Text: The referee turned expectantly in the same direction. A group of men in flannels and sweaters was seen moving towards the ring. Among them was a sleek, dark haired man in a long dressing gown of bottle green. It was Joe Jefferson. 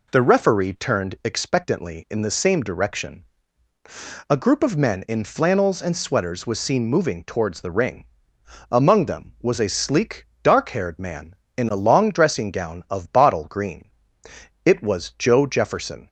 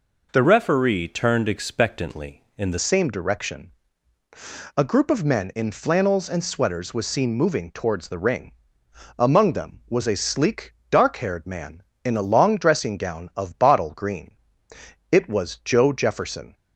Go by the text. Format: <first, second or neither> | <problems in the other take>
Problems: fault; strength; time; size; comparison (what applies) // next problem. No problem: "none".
first | changes voice from "referee" to "the"; from 0.4 to 2.7 s; 2.3 s long